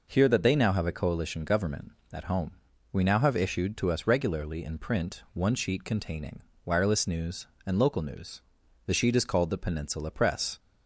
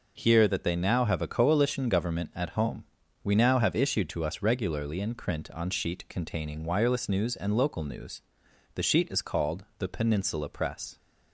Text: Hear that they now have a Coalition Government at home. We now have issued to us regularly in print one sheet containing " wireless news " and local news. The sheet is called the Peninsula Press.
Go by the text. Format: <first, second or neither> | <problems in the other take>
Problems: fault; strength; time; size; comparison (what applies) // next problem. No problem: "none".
first | says "on" for "one"; at 5.5 s